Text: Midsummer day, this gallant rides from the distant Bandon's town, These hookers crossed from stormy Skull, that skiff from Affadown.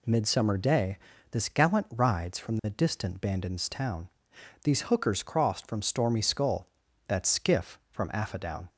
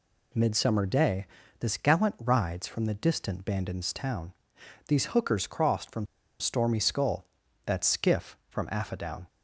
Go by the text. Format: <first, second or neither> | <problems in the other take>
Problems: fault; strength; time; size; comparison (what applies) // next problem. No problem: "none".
first | pauses between "from" and "stormy"; slight; at 6.0 s; 0.34 s long